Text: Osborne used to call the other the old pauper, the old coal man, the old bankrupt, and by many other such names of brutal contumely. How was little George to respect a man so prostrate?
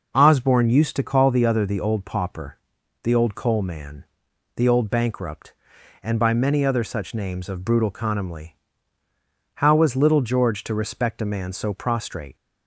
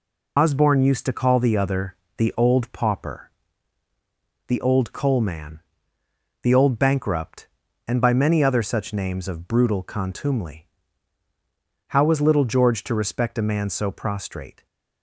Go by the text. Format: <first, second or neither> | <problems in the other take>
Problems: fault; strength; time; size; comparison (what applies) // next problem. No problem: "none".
first | loses the start of "Osborne"; at 0.3 s; 90 ms // pauses between "other" and "the"; slight; at 1.9 s; 0.24 s long